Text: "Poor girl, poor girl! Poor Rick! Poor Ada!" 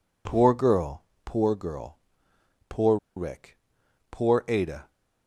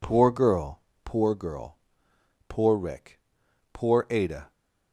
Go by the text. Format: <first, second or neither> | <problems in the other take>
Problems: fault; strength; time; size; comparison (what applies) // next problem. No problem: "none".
second | pauses between "Poor" and "Rick"; slight; at 2.9 s; 0.20 s long